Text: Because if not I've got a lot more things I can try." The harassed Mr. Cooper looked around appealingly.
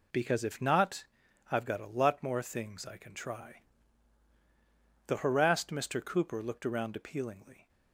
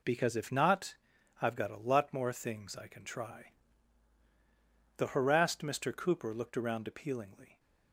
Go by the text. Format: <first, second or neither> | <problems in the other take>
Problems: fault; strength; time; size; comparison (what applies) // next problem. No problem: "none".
neither | pauses between "not" and "I've"; the same in both